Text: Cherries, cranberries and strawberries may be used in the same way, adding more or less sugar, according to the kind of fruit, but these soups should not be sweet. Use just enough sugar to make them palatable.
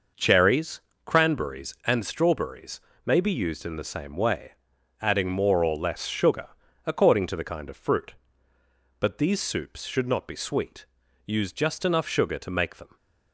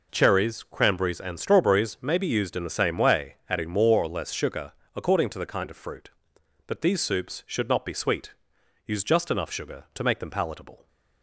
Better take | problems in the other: second | pauses between "strawberries" and "may"; slight; at 2.7 s; 0.26 s long // stops before "palatable"; at 12.9 s

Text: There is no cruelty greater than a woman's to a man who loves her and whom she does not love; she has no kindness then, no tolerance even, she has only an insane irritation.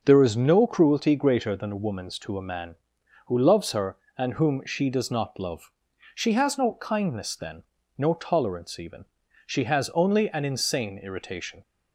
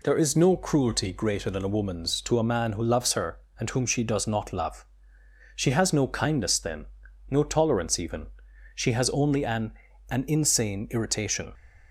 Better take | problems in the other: first | says "an" twice; at 10.0 s

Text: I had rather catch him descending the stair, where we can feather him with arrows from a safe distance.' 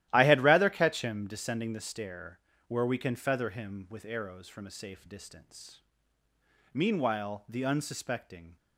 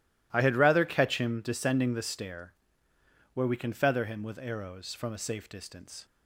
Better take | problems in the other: second | starts louder than the rest; strong; until 1.1 s; 14 dB // goes on to say "Meanwhile the unsuspecting"; strong; from 6.7 s on; 1.8 s long

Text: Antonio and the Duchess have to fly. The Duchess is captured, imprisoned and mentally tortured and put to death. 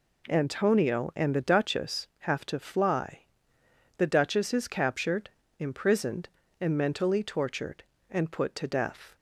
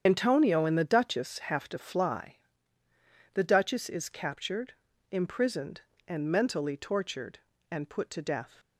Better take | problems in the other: first | loses the start of "Antonio"; at 0.0 s; 65 ms // starts louder than the rest; strong; until 1.0 s; 8 dB

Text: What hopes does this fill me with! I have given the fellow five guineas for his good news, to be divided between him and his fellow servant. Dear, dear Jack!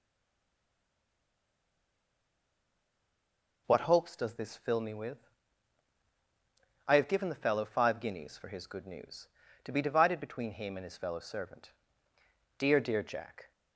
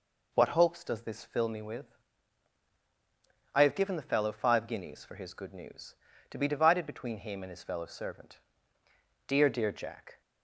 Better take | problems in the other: second | stays silent before the first word; strong; until 3.6 s; 3.6 s long

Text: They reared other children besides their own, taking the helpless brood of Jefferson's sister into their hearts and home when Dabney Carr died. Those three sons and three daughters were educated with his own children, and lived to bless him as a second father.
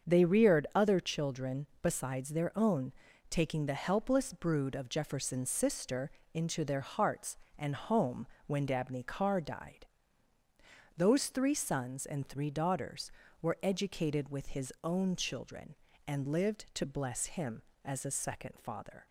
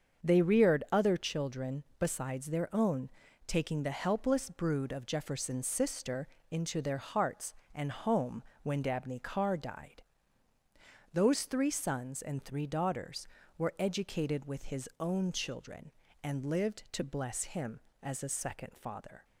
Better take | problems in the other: neither | starts louder than the rest; the same in both // pauses between "children" and "besides"; slight; the same in both // pauses between "sister" and "into"; slight; the same in both // pauses between "home" and "when"; slight; the same in both

